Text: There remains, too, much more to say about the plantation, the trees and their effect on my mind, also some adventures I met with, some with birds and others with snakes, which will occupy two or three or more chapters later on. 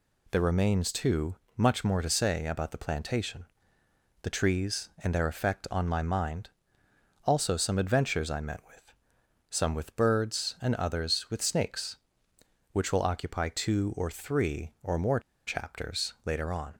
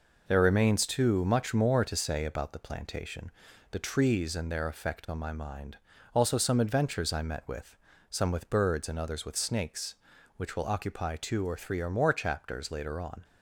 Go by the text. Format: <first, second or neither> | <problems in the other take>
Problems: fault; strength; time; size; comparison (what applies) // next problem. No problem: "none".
second | pauses between "more" and "chapters"; slight; at 15.1 s; 0.27 s long